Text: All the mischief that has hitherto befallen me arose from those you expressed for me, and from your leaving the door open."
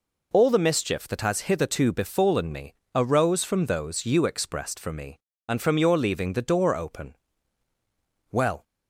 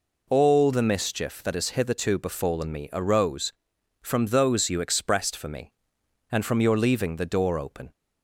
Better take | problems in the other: second | pauses between "me" and "arose"; slight; at 2.7 s; 0.22 s long // goes on to say "Well"; slight; from 8.3 s on; 0.32 s long

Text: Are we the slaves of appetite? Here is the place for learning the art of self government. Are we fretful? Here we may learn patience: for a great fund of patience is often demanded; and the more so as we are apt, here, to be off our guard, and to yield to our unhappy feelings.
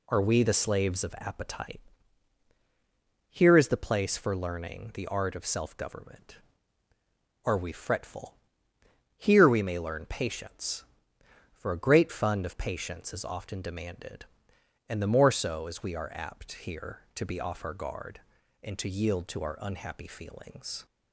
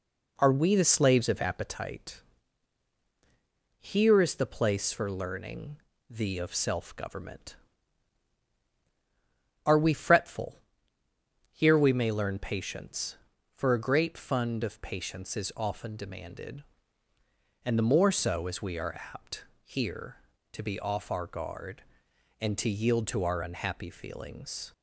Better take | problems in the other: first | pauses between "learning" and "the"; slight; at 5.7 s; 0.32 s long // skips "art"; at 6.3 s // pauses between "are" and "apt"; slight; at 18.9 s; 0.16 s long

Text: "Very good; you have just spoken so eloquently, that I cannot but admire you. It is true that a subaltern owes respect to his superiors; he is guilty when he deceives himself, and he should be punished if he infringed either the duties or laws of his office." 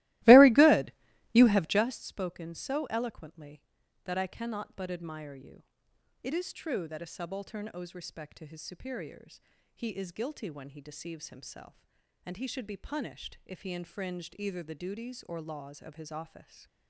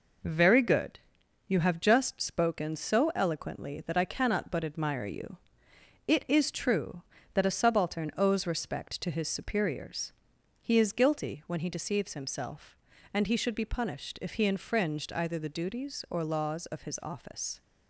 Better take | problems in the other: second | starts louder than the rest; strong; until 2.0 s; 18.5 dB

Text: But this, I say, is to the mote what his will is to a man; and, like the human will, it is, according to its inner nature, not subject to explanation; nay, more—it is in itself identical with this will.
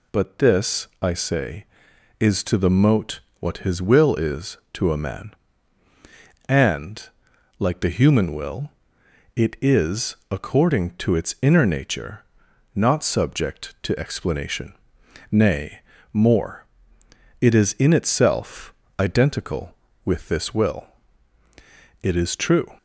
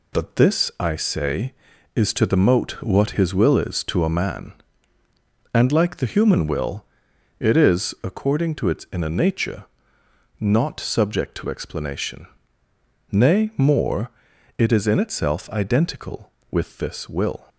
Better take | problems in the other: second | pauses between "mote" and "what"; slight; at 3.1 s; 0.20 s long // pauses between "itself" and "identical"; slight; at 18.7 s; 0.26 s long // goes on to say "It is true"; noticeable; from 22.0 s on; 0.74 s long

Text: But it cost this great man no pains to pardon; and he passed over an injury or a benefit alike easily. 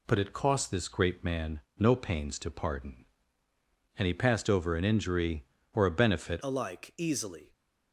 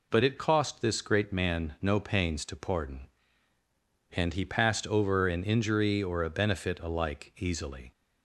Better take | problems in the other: second | pauses between "man" and "no"; slight; at 1.6 s; 0.18 s long // changes voice at "alike"; from 6.4 s on; 1.1 s long

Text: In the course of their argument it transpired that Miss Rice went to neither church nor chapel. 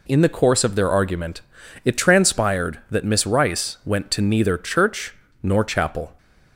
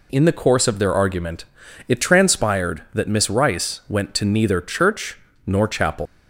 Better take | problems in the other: first | pauses between "argument" and "it"; at 1.4 s; 0.42 s long; also in the first // pauses between "church" and "nor"; slight; at 5.1 s; 0.30 s long; slight in the first // leaves "chapel" unfinished; at 6.0 s; 150 ms

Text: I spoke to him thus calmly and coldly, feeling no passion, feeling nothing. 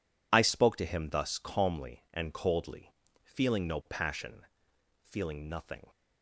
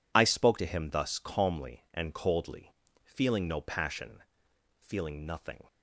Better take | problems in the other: neither | none

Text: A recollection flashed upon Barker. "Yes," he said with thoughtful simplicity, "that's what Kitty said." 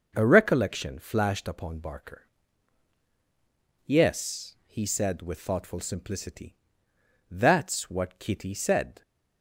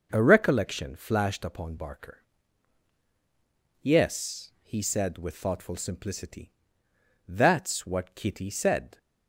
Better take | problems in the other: neither | none

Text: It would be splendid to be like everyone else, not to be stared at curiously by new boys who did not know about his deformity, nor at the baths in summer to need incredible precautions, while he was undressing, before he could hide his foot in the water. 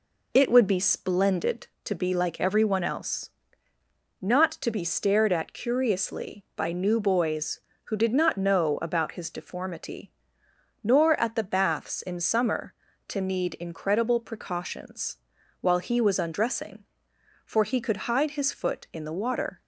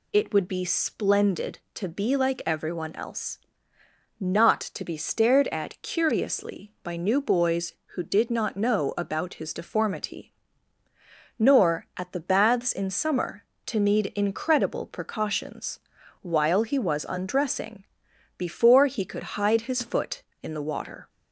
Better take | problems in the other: second | says "for" for "before"; at 17.4 s

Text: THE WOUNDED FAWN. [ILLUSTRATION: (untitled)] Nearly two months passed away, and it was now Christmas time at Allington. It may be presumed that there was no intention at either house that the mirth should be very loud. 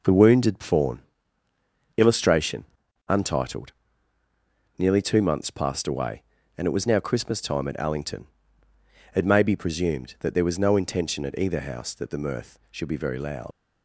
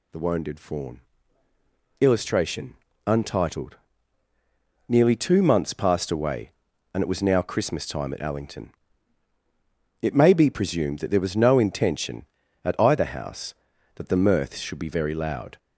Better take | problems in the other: second | leaves "loud" unfinished; at 13.5 s; 80 ms

